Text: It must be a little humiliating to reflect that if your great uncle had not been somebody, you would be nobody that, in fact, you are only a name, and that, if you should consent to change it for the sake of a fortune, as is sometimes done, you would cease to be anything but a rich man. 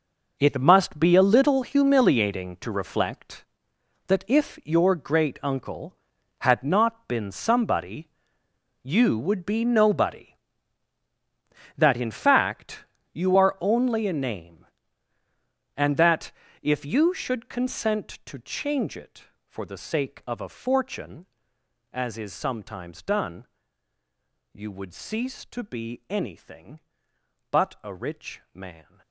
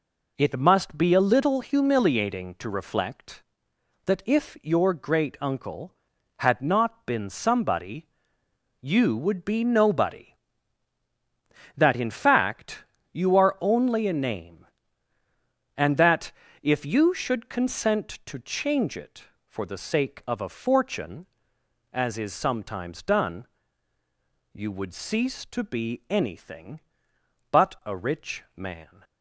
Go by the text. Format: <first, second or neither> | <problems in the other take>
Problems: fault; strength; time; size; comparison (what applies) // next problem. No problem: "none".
second | gets quieter; strong; throughout; 12.5 dB